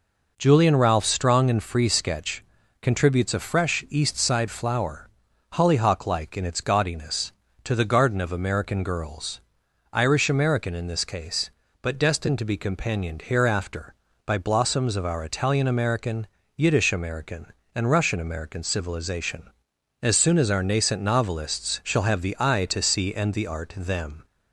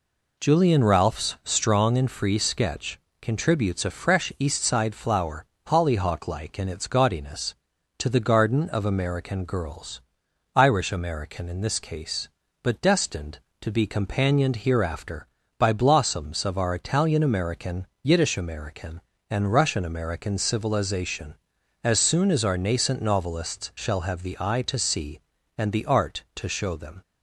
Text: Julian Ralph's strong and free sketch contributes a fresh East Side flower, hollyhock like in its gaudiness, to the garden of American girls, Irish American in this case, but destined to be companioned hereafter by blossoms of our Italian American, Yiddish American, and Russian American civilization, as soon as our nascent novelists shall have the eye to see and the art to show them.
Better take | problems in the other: second | pauses between "sketch" and "contributes"; at 2.4 s; 0.38 s long; slight in the second // skips "to show"; at 23.7 s

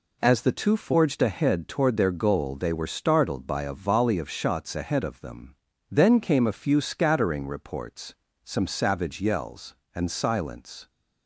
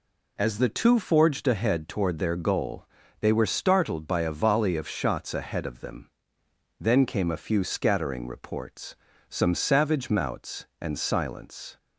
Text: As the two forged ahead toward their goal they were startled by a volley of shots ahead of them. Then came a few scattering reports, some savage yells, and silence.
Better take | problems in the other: first | pauses between "goal" and "they"; slight; at 2.8 s; 0.36 s long // says "mouts" for "yells"; at 10.1 s

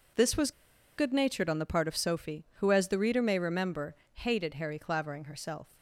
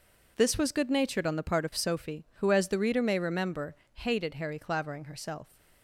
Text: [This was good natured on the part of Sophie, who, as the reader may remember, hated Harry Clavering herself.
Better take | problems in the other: second | pauses between "was" and "good"; at 0.5 s; 0.45 s long

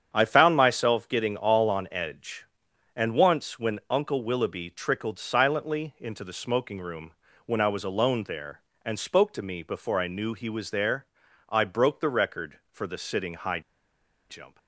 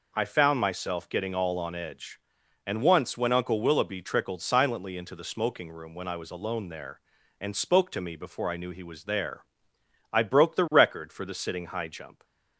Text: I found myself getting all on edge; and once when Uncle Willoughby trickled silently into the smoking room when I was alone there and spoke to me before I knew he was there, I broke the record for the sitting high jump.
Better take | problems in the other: second | starts louder than the rest; strong; until 1.1 s; 8 dB // pauses between "room" and "when"; slight; at 7.1 s; 0.34 s long // pauses between "high" and "jump"; noticeable; at 13.6 s; 0.69 s long

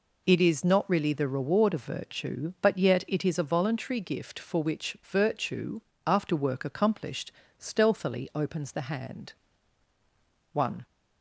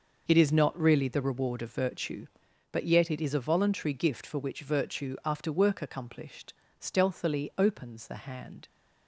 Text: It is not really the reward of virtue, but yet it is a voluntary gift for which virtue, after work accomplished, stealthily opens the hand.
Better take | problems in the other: second | goes on to say "One"; slight; from 10.5 s on; 0.32 s long

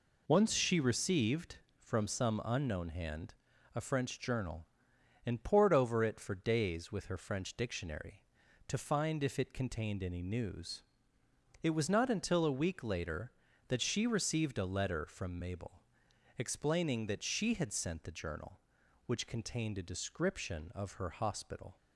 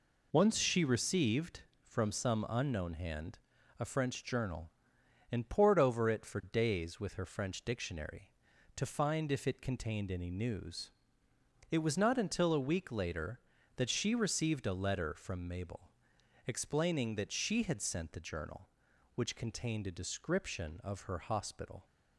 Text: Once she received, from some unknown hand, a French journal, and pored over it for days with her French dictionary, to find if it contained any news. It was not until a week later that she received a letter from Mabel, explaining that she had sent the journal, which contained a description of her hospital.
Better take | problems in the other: neither | none

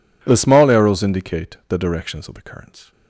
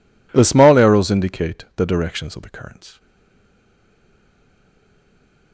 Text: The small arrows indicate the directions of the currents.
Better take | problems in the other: first | stays silent after the last word; strong; from 2.9 s on; 2.6 s long

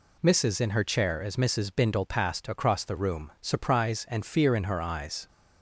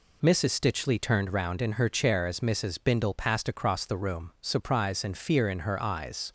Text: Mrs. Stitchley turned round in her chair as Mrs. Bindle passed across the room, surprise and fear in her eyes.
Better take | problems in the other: second | skips "Stitchley turned round"; at 0.5 s

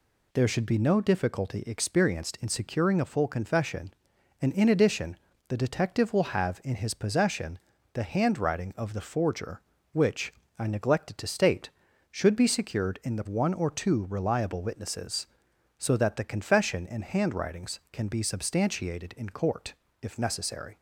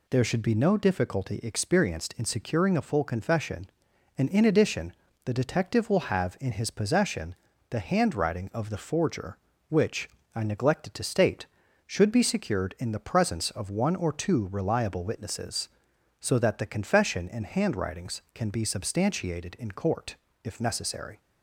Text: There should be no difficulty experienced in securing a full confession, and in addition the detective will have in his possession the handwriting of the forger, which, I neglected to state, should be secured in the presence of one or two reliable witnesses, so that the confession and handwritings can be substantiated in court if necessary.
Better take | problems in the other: second | pauses between "addition" and "the"; slight; at 5.1 s; 0.32 s long; slight in the second // pauses between "possession" and "the"; slight; at 7.5 s; 0.36 s long; slight in the second // skips "presence of"; at 13.2 s // pauses between "court" and "if"; slight; at 19.7 s; 0.30 s long; slight in the second

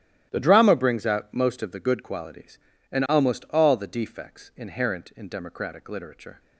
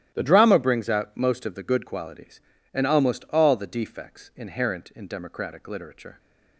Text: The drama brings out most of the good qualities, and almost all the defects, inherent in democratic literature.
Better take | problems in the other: neither | starts louder than the rest; strong; the same in both

